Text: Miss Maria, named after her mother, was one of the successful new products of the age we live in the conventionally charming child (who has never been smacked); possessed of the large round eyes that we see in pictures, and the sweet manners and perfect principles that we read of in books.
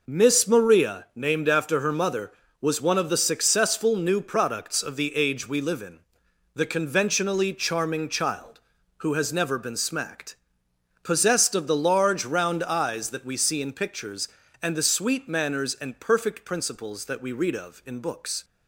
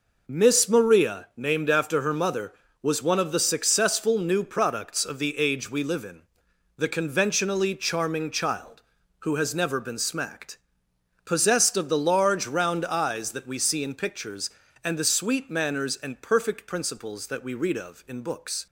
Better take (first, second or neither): neither